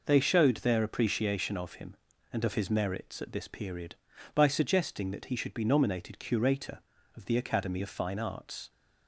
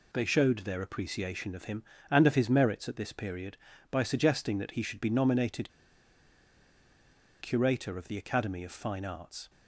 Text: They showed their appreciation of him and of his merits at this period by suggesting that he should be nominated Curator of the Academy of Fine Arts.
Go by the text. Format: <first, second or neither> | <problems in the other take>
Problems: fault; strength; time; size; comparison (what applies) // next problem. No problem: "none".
first | pauses between "nominated" and "Curator"; strong; at 5.7 s; 1.7 s long